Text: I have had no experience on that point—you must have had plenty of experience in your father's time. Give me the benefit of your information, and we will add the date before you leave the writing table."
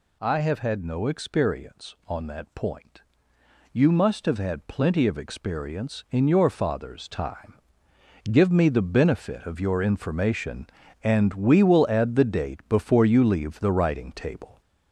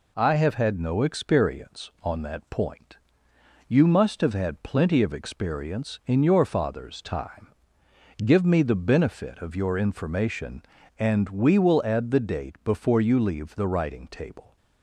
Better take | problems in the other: second | gets louder; noticeable; throughout; 5.5 dB

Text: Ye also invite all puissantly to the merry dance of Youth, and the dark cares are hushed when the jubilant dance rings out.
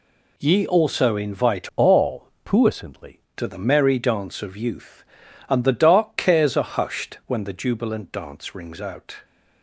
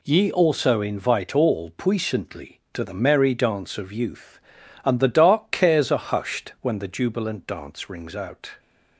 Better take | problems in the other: second | changes voice from "all" to "puissantly"; from 1.7 to 3.1 s; 1.4 s long // pauses between "all" and "puissantly"; slight; at 2.2 s; 0.16 s long

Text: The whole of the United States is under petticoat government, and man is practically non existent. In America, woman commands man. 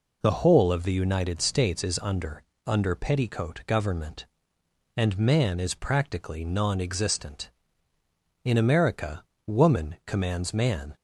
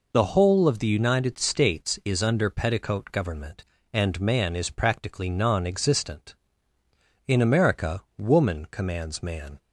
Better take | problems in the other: second | says "under" twice; at 2.6 s

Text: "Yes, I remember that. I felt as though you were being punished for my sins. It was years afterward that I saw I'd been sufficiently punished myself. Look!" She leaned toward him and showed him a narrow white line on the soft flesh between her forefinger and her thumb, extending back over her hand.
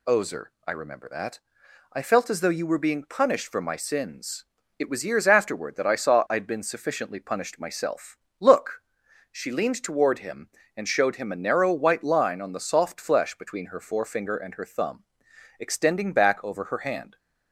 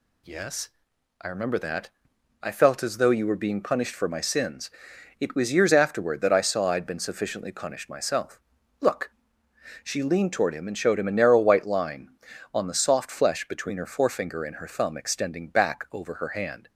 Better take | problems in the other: second | says "Ozer" for "Yes"; at 0.0 s

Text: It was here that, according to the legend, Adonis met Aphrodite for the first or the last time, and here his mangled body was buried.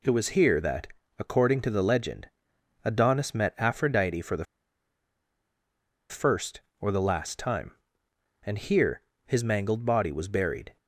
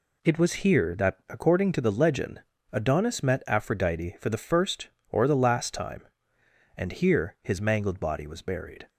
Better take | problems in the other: second | pauses between "the" and "first"; strong; at 4.4 s; 1.6 s long // pauses between "here" and "his"; slight; at 9.0 s; 0.24 s long

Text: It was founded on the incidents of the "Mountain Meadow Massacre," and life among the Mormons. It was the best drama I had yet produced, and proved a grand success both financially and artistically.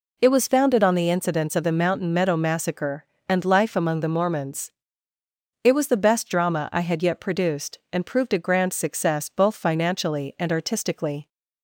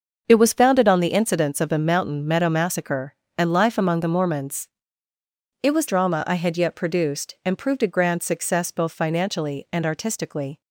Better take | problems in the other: first | starts louder than the rest; until 1.2 s; 6.5 dB // skips "the best"; at 5.8 s

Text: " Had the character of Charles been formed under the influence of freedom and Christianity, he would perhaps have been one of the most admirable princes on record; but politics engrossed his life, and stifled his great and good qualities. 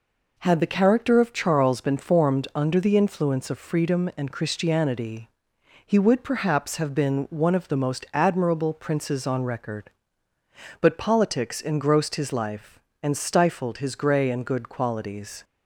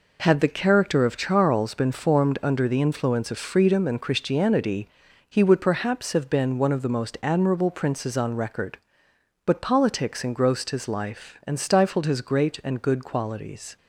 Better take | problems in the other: second | says "grey" for "great"; at 13.9 s

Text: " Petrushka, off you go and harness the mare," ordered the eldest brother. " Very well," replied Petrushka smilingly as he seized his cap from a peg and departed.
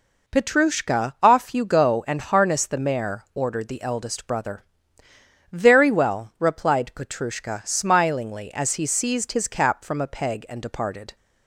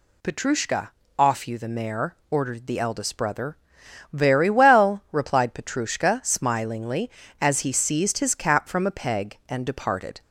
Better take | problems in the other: first | skips "go and harness"; at 1.5 s

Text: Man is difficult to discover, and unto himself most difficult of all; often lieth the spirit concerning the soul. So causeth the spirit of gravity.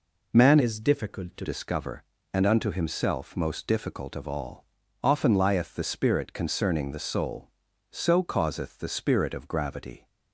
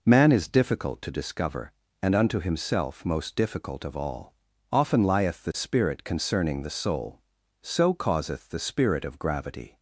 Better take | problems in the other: second | changes voice from "is" to "to"; from 0.5 to 1.4 s; 0.9 s long

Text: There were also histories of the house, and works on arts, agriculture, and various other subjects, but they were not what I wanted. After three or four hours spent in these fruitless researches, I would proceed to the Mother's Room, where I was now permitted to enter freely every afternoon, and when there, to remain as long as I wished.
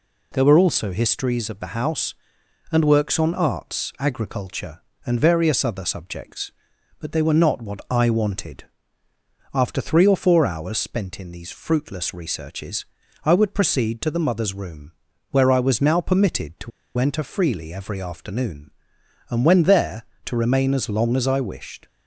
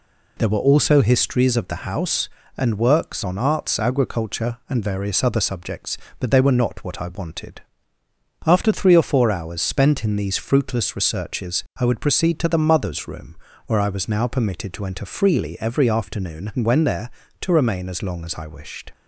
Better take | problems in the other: second | pauses between "to" and "enter"; slight; at 16.7 s; 0.27 s long

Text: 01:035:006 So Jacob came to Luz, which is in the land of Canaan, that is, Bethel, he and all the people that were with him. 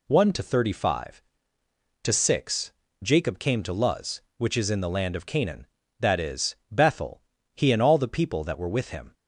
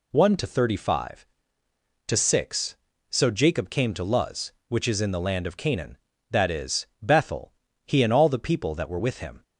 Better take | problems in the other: second | skips "So"; at 2.8 s

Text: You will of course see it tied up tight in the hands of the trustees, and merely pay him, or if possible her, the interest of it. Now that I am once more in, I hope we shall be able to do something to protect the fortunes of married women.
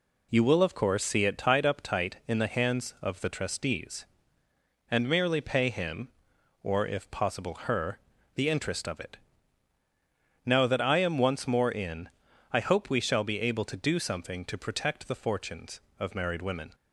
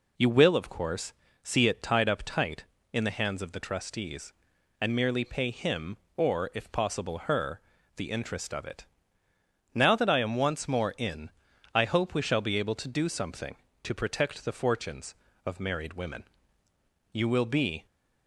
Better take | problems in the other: first | pauses between "course" and "see"; slight; at 1.1 s; 0.32 s long // goes on to say "You will be"; noticeable; from 17.1 s on; 0.74 s long

